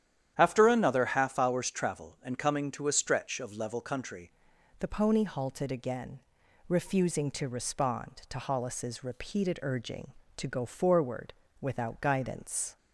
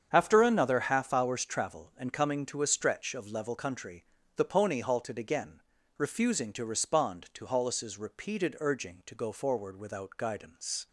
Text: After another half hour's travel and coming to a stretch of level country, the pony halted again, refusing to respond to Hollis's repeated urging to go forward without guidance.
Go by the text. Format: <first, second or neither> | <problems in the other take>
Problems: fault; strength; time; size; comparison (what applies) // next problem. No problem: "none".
second | starts louder than the rest; strong; until 1.3 s; 10.5 dB; strong in the second // changes voice at "the"; from 4.7 s on; 8.0 s long // pauses between "forward" and "without"; slight; at 11.3 s; 0.28 s long